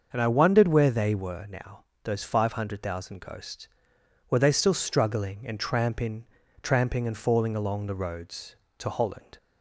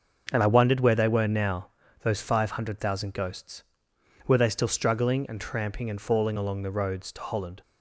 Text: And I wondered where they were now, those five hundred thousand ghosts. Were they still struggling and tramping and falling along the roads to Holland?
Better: second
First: starts louder than the rest; until 1.1 s; 6.5 dB // says "tramping" twice; at 6.6 s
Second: starts louder than the rest; until 1.3 s; 6.5 dB

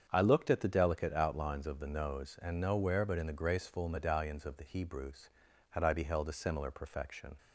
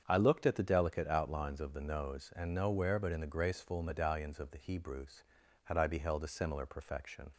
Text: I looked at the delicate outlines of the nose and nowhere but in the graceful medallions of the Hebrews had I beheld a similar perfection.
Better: neither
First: starts louder than the rest; strong; until 1.1 s; 7.5 dB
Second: starts louder than the rest; strong; until 1.0 s; 7.5 dB

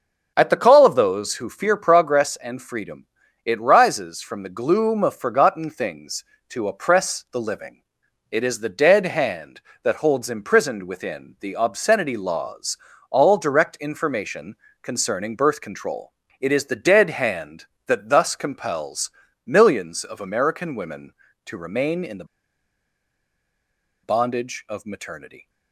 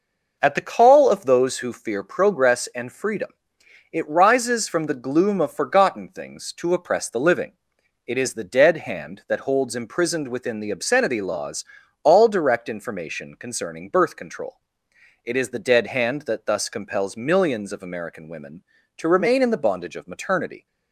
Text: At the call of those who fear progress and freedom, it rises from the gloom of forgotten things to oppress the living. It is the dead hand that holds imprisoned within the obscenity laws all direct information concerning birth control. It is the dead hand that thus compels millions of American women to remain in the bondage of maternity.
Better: second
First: starts louder than the rest; until 1.3 s; 6 dB // pauses between "laws" and "all"; slight; at 12.7 s; 0.32 s long // pauses between "information" and "concerning"; slight; at 14.5 s; 0.26 s long // pauses between "compels" and "millions"; slight; at 19.1 s; 0.34 s long // pauses between "the" and "bondage"; strong; at 22.2 s; 1.7 s long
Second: pauses between "laws" and "all"; at 11.6 s; 0.40 s long

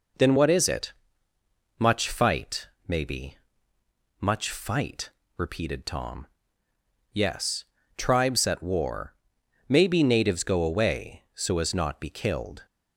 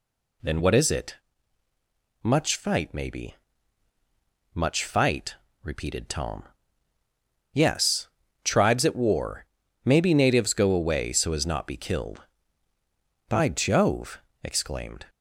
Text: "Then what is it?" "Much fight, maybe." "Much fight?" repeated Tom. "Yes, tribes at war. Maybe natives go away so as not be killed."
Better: first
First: none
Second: goes on to say "By Jove exclaimed"; strong; from 13.2 s on; 1.7 s long

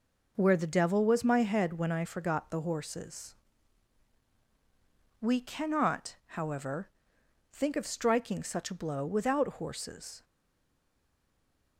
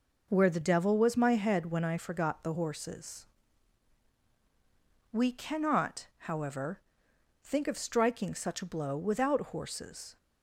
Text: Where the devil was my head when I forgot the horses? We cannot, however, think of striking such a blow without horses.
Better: second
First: stays silent after the last word; noticeable; from 10.2 s on; 1.5 s long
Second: none

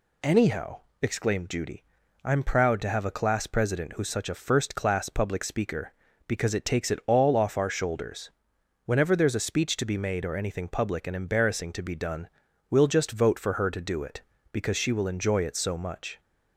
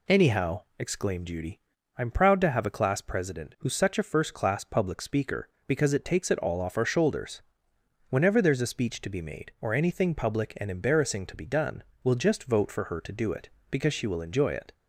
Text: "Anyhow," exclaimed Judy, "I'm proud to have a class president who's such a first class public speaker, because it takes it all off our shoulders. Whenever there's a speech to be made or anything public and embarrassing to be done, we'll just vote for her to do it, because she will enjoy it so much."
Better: first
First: none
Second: stops before "so much"; at 14.7 s

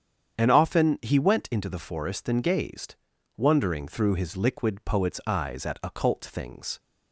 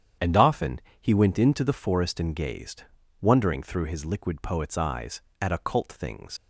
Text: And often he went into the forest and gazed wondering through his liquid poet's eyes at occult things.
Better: first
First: starts louder than the rest; strong; until 1.3 s; 8 dB // pauses between "gazed" and "wondering"; at 2.9 s; 0.42 s long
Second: starts louder than the rest; strong; until 1.4 s; 8.5 dB // pauses between "often" and "he"; slight; at 0.8 s; 0.20 s long // pauses between "gazed" and "wondering"; slight; at 2.8 s; 0.36 s long // leaves "things" unfinished; at 6.3 s; 75 ms

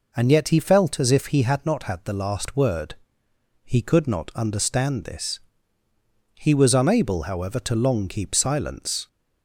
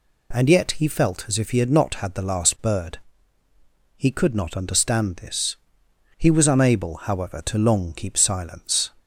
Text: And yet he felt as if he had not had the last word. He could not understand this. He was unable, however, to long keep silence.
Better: first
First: none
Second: says "bird" for "word"; at 2.6 s

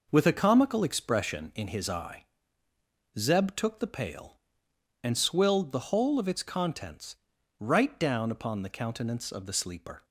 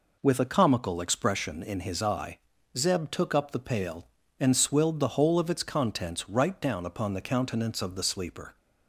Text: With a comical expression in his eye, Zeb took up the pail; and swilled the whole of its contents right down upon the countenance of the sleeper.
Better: second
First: skips "up"; at 3.7 s // pauses between "contents" and "right"; at 7.1 s; 0.44 s long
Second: none

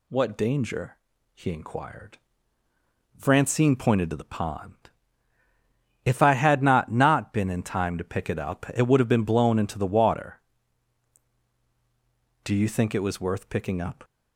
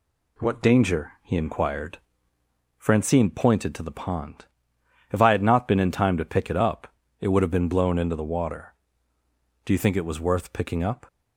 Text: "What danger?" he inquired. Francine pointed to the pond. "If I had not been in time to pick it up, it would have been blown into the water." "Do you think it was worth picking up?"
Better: second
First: says "not" twice; at 6.9 s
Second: none

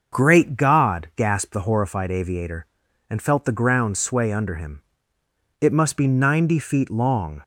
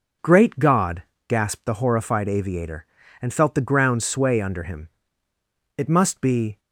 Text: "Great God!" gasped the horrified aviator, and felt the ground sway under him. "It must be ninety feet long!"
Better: first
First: none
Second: stops before "ninety feet long"; at 6.5 s

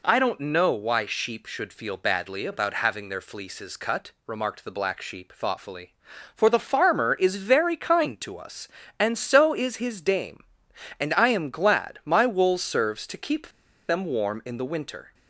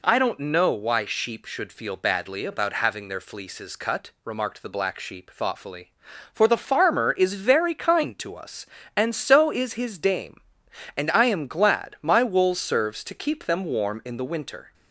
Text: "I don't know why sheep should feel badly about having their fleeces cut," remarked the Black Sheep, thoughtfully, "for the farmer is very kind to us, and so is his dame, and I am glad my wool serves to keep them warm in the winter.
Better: second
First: pauses between "keep" and "them"; at 13.4 s; 0.40 s long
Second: none

